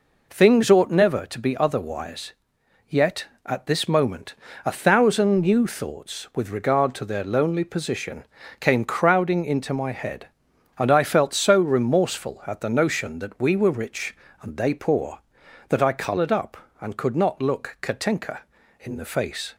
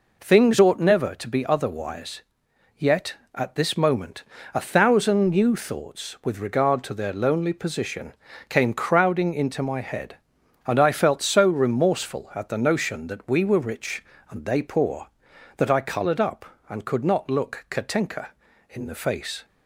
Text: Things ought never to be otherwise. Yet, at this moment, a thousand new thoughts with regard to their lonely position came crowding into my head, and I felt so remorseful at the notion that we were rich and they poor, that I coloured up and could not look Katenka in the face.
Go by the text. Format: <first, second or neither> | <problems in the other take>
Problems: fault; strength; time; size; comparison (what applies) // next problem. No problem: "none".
neither | pauses between "position" and "came"; slight; the same in both